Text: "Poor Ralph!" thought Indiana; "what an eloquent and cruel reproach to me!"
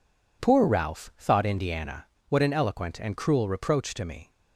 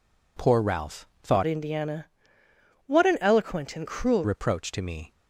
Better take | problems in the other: first | changes voice from "Indiana" to "cruel"; from 1.4 to 4.2 s; 2.8 s long

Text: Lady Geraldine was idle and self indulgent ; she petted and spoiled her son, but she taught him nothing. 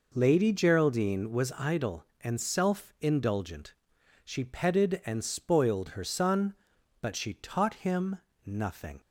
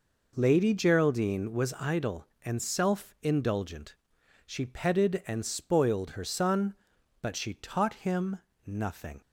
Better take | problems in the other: neither | pauses between "him" and "nothing"; slight; the same in both

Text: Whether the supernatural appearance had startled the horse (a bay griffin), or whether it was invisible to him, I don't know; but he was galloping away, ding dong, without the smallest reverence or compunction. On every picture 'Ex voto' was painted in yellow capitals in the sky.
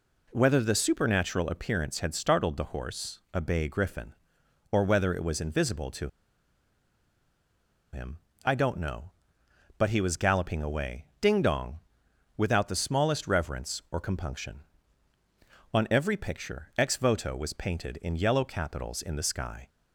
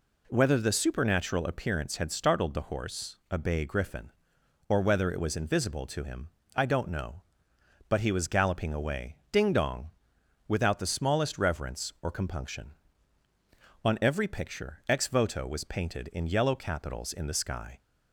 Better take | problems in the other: second | pauses between "to" and "him"; strong; at 6.0 s; 1.8 s long

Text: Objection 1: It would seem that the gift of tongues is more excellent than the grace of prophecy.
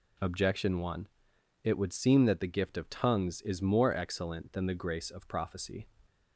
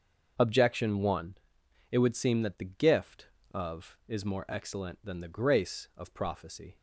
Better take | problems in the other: first | starts louder than the rest; until 1.3 s; 6.5 dB // skips "tongues"; at 4.0 s

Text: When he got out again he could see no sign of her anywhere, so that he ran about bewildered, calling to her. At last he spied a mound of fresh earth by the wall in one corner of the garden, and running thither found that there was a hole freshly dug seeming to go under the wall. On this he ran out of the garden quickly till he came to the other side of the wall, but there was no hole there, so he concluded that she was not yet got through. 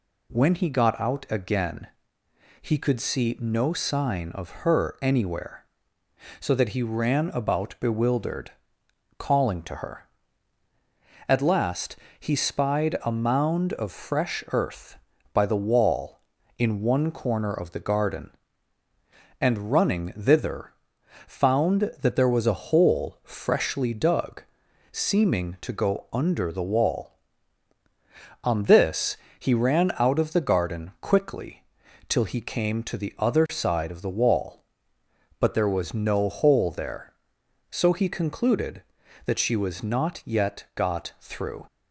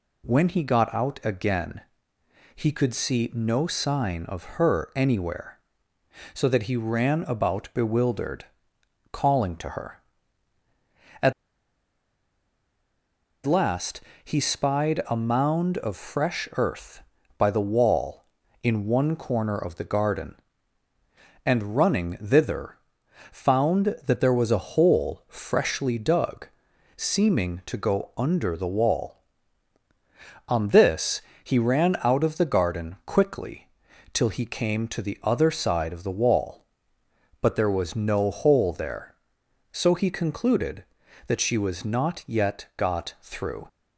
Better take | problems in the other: first | pauses between "again" and "he"; noticeable; at 1.8 s; 0.74 s long; noticeable in the first // pauses between "of" and "her"; slight; at 4.4 s; 0.16 s long; slight in the first // pauses between "At" and "last"; strong; at 11.3 s; 2.1 s long // pauses between "last" and "he"; slight; at 14.0 s; 0.22 s long; slight in the first // pauses between "thither" and "found"; noticeable; at 22.7 s; 0.56 s long; noticeable in the first // pauses between "dug" and "seeming"; noticeable; at 26.4 s; 0.50 s long; noticeable in the first // pauses between "this" and "he"; slight; at 31.2 s; 0.22 s long; slight in the first // pauses between "quickly" and "till"; noticeable; at 33.6 s; 0.46 s long; noticeable in the first

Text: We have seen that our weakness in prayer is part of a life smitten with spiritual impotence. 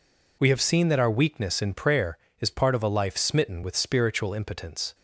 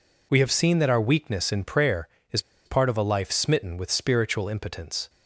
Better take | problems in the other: first | pauses between "is" and "part"; slight; at 2.4 s; 0.24 s long

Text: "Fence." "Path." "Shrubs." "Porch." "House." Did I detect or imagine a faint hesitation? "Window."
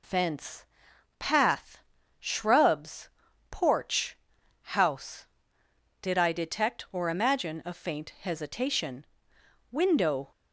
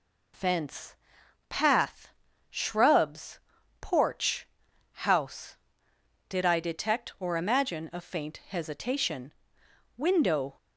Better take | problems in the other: neither | none

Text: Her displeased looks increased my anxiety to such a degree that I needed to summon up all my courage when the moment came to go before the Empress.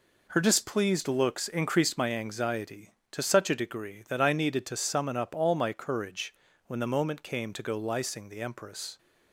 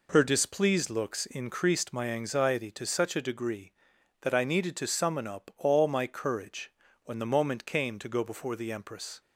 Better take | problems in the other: second | pauses between "courage" and "when"; slight; at 6.3 s; 0.32 s long; slight in the second // says "lysing" for "before"; at 7.7 s

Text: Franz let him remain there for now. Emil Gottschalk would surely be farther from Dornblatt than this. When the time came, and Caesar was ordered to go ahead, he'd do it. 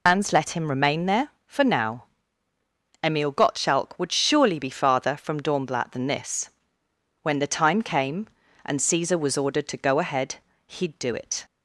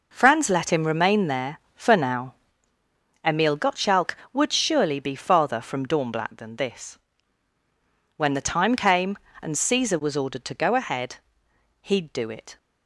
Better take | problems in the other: second | loses the start of "Franz"; at 0.0 s; 115 ms

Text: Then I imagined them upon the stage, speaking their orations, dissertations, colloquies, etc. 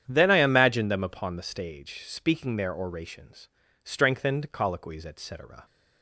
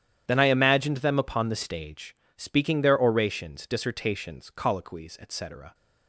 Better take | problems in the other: second | starts louder than the rest; strong; until 1.0 s; 9 dB; strong in the second // says "strengthened" for "dissertations"; at 3.8 s

